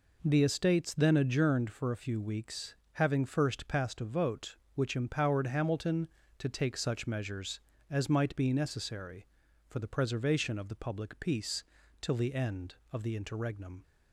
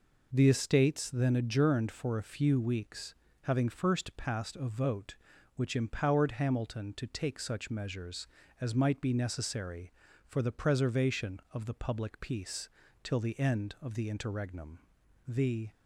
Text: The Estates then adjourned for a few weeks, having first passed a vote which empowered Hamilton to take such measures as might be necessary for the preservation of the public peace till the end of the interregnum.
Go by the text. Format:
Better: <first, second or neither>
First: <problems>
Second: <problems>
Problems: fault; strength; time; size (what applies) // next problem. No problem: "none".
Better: first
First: pauses between "peace" and "till"; at 11.6 s; 0.40 s long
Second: pauses between "peace" and "till"; slight; at 12.6 s; 0.34 s long // goes on to say "The"; slight; from 15.2 s on; 0.44 s long